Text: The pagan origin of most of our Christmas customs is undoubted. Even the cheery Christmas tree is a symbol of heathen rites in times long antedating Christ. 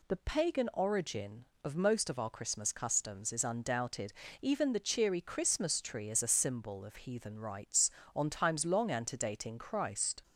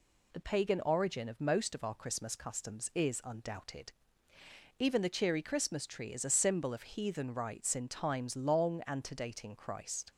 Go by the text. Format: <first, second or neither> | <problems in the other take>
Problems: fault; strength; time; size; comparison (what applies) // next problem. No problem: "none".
second | says "on" for "in"; at 8.1 s